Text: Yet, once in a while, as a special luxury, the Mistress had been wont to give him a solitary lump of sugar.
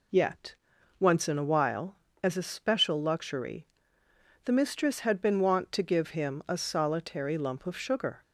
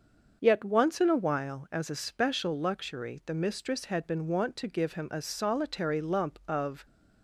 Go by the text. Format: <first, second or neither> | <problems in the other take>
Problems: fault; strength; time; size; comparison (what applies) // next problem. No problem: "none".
first | starts louder than the rest; until 1.4 s; 6.5 dB // stops before "sugar"; at 6.8 s